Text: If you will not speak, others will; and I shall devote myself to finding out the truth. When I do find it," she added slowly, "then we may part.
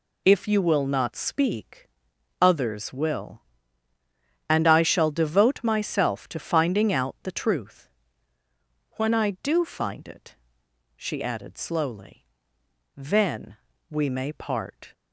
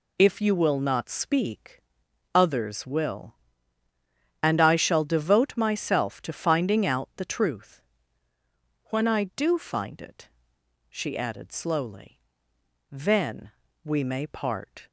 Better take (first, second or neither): neither